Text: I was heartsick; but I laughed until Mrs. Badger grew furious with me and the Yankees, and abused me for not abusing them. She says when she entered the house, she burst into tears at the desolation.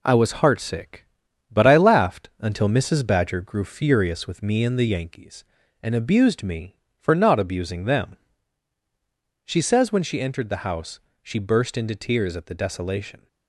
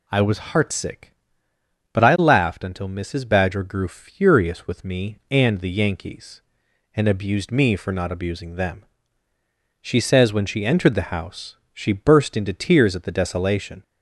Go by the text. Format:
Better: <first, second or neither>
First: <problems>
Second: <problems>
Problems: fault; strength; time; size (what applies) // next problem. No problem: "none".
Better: second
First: gets quieter; noticeable; throughout; 5.5 dB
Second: none